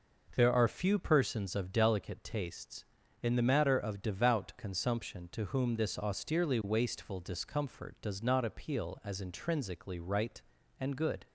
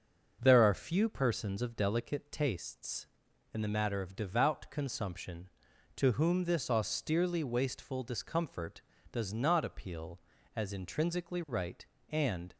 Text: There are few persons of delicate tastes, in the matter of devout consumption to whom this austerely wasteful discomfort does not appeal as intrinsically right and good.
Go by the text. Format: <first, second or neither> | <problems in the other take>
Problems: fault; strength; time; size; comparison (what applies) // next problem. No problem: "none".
first | starts louder than the rest; until 1.4 s; 6 dB // stops before "good"; at 12.5 s